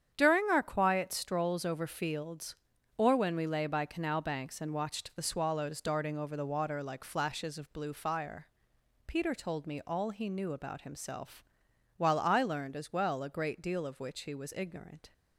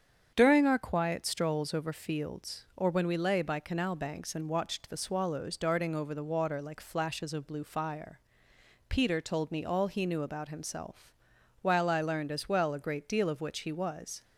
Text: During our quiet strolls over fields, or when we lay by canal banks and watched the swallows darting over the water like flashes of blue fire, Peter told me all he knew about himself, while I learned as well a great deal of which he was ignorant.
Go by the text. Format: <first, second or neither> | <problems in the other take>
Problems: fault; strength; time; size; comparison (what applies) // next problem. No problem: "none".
first | starts louder than the rest; strong; until 1.3 s; 7.5 dB; strong in the first // stops before "ignorant"; at 14.2 s